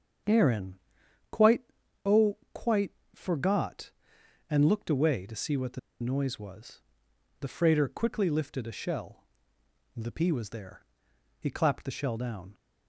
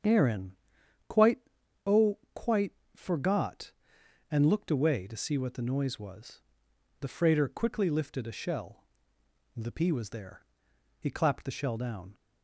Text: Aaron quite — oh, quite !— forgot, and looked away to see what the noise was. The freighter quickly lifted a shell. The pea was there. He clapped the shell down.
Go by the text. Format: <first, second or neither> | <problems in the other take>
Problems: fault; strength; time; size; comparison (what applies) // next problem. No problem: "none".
second | starts louder than the rest; strong; until 2.2 s; 8 dB; strong in the second // pauses between "Aaron" and "quite"; noticeable; at 0.7 s; 0.52 s long; noticeable in the second // pauses between "the" and "noise"; slight; at 5.7 s; 0.22 s long